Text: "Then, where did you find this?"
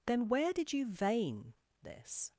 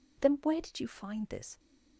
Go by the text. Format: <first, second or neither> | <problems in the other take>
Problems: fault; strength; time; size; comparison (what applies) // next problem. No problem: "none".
second | says "vein" for "find"; at 0.8 s